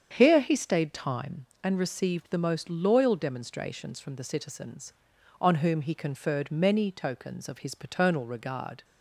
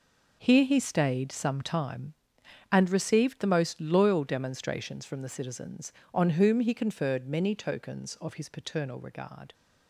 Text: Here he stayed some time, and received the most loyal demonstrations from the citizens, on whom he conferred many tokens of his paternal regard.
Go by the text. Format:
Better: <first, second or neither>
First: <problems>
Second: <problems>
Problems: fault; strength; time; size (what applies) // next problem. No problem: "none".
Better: second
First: starts louder than the rest; strong; until 1.1 s; 7.5 dB // skips "some"; at 0.9 s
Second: none